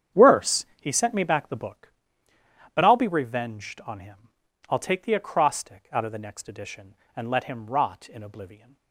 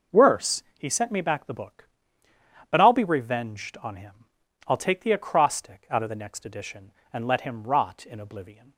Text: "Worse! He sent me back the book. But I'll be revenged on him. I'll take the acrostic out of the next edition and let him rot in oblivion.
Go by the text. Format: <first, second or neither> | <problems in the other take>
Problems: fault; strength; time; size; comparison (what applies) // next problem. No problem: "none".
second | starts louder than the rest; strong; until 1.8 s; 8.5 dB